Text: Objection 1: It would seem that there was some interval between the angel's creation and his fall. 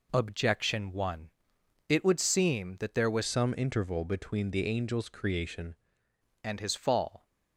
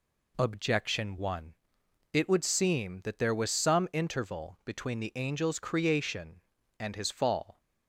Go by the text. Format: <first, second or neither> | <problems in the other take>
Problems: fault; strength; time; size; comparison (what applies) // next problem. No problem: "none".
second | changes voice from "some" to "creation"; from 3.2 to 5.7 s; 2.5 s long